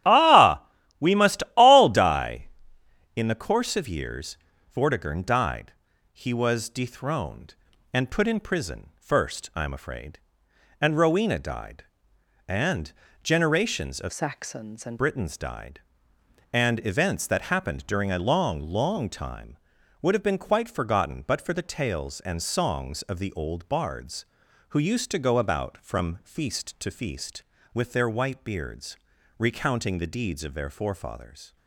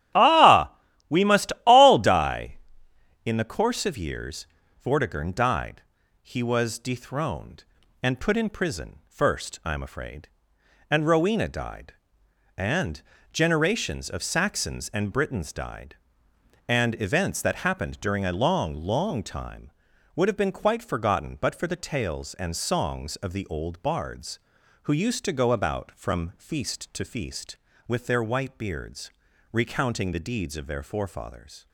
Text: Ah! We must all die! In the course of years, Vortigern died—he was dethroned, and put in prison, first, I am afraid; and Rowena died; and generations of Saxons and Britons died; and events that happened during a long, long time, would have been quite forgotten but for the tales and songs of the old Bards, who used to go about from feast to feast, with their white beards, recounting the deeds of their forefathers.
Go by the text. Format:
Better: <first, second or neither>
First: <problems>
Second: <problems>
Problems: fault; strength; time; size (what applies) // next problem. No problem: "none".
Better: second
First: starts louder than the rest; strong; until 1.4 s; 11.5 dB // pauses between "and" and "generations"; slight; at 12.9 s; 0.30 s long // changes voice from "Saxons" to "and"; from 14.1 to 15.0 s; 0.9 s long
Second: starts louder than the rest; strong; until 1.5 s; 11.5 dB // pauses between "and" and "generations"; slight; at 13.0 s; 0.30 s long